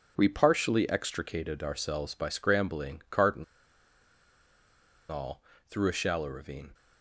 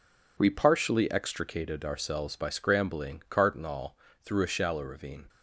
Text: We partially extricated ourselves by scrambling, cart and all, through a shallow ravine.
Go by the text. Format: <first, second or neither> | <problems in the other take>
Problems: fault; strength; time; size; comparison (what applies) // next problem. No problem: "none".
second | pauses between "and" and "all"; strong; at 3.4 s; 1.6 s long